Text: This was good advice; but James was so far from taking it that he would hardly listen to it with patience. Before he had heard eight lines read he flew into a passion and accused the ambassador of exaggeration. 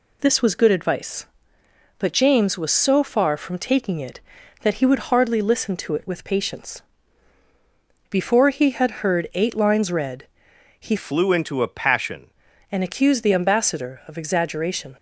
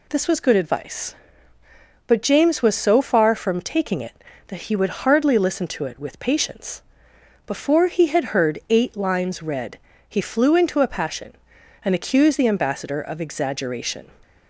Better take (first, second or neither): second